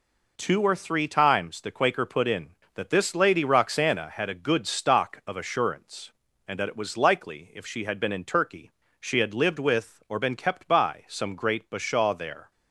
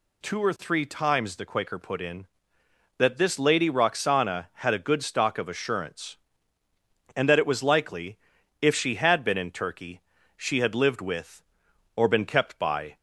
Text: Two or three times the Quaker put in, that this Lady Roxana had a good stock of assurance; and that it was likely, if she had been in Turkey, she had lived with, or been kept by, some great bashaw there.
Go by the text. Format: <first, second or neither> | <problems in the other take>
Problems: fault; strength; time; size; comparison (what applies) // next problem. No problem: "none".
first | stops before "some great bashaw there"; at 12.9 s